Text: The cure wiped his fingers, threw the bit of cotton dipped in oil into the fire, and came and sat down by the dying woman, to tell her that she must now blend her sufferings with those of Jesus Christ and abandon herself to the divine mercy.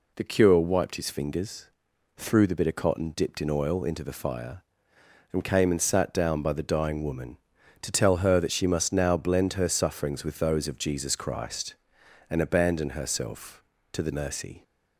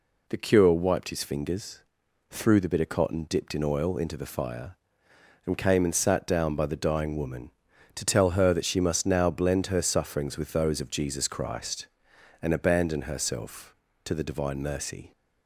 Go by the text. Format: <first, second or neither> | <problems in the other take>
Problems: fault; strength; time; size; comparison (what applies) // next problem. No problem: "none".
second | skips "divine"; at 14.1 s